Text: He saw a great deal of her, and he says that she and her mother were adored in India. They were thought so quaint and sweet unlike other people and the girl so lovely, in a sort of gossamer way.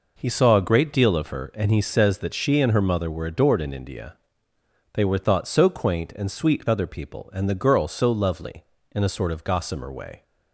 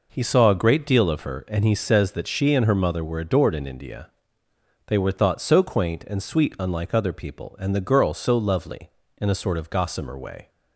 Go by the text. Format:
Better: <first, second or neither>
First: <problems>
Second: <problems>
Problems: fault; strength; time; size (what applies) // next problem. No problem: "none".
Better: second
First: skips "unlike"; at 6.6 s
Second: none